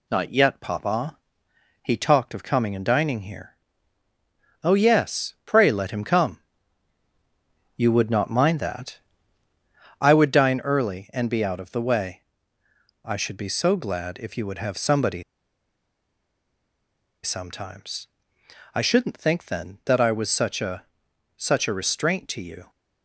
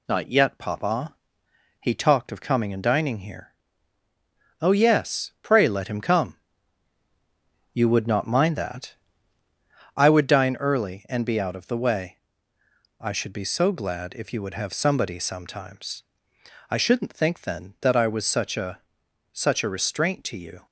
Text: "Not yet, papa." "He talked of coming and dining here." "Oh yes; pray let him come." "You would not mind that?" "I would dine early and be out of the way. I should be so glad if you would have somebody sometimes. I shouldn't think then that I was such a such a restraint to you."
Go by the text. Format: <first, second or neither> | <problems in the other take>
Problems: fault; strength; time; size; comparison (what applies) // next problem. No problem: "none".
second | pauses between "somebody" and "sometimes"; strong; at 15.2 s; 2.0 s long // pauses between "a" and "such"; noticeable; at 20.8 s; 0.52 s long; noticeable in the second